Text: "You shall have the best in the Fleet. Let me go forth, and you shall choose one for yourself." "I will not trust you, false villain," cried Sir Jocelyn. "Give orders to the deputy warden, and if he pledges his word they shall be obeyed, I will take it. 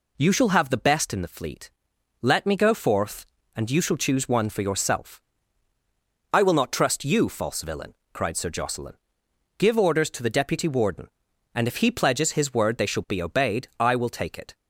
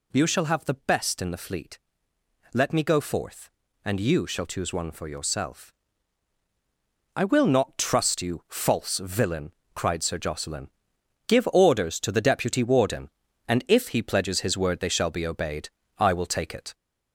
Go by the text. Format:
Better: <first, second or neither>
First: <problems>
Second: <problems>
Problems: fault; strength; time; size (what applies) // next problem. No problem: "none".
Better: first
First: none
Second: gets louder; throughout; 4 dB